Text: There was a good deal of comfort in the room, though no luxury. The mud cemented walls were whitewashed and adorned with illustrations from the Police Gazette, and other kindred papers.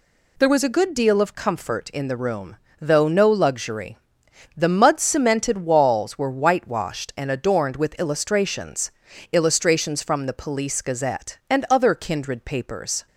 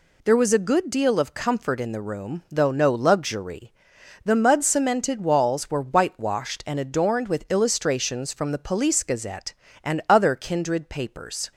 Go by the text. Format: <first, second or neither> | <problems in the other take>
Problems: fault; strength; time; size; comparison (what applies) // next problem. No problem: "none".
second | says "illustrations" twice; at 9.3 s